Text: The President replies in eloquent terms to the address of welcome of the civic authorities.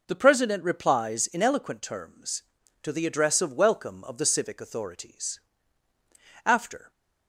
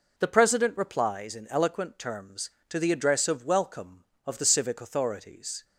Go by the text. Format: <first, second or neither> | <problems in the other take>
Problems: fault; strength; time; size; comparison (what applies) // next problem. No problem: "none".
second | goes on to say "After"; slight; from 6.4 s on; 0.46 s long